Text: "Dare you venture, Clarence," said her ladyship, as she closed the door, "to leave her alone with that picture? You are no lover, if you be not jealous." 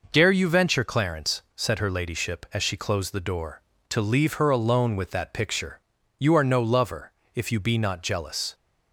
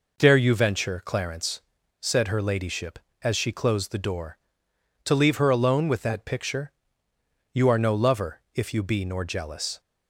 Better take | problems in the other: first | says "nor" for "not"; at 9.0 s

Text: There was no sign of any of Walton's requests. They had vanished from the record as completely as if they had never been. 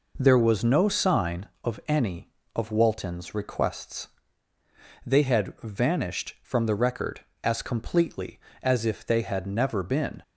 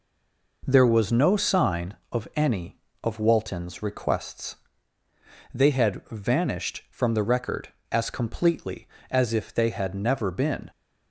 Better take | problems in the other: first | stays silent before the first word; slight; until 0.6 s; 0.6 s long

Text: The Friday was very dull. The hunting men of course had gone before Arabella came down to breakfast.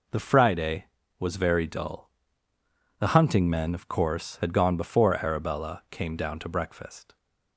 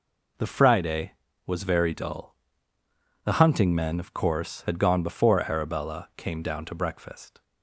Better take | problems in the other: neither | none

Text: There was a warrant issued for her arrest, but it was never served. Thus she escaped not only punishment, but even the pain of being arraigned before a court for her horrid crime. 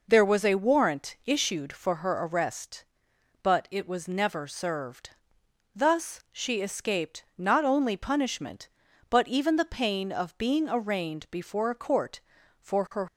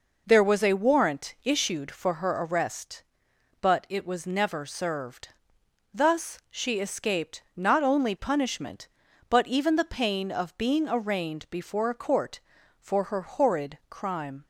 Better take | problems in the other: second | stops before "horrid crime"; at 13.0 s

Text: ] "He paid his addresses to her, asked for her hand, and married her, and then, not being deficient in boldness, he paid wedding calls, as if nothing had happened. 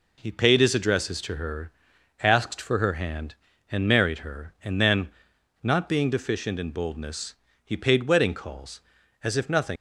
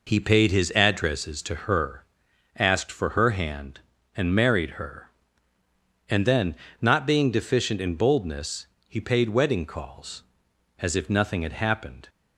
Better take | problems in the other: second | stops before "had happened"; at 9.7 s

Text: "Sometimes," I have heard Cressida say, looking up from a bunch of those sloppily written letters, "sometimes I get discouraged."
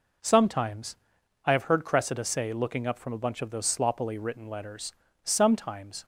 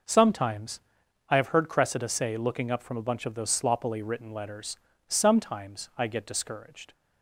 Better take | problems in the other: second | stops before "I get discouraged"; at 6.0 s

